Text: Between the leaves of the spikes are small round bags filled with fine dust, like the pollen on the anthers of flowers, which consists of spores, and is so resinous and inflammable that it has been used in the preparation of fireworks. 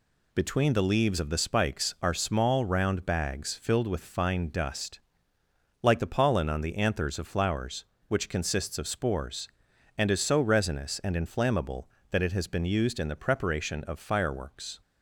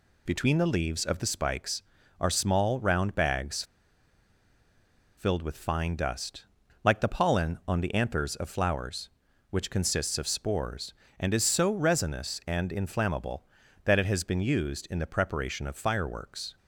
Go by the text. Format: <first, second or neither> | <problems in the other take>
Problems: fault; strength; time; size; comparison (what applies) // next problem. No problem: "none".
first | pauses between "bags" and "filled"; strong; at 3.6 s; 1.5 s long